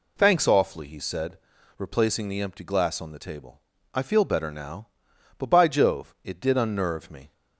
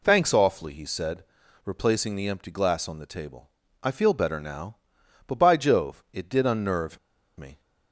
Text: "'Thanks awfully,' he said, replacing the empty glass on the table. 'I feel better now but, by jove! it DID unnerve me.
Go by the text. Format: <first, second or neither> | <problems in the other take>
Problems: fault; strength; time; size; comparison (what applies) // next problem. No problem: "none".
first | pauses between "unnerve" and "me"; at 6.9 s; 0.39 s long